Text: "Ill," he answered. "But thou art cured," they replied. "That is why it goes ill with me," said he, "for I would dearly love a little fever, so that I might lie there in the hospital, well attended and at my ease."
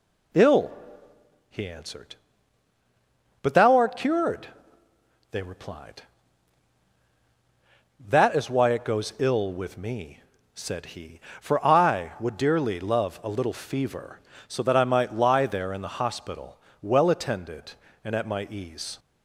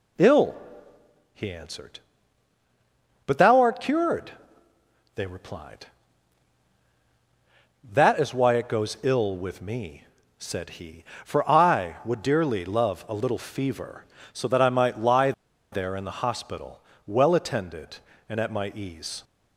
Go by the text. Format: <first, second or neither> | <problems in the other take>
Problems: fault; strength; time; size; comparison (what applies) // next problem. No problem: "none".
first | pauses between "lie" and "there"; at 15.3 s; 0.40 s long